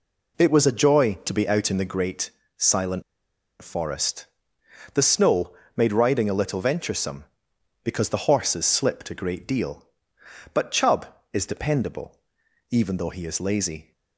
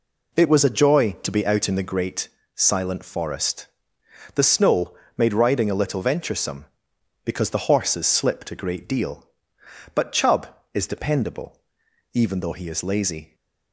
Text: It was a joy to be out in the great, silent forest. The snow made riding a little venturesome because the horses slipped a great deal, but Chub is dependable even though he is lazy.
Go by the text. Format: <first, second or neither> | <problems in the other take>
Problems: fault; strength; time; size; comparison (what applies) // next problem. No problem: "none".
second | pauses between "silent" and "forest"; noticeable; at 3.0 s; 0.59 s long // pauses between "snow" and "made"; slight; at 5.5 s; 0.24 s long; slight in the second // pauses between "dependable" and "even"; noticeable; at 12.1 s; 0.56 s long; noticeable in the second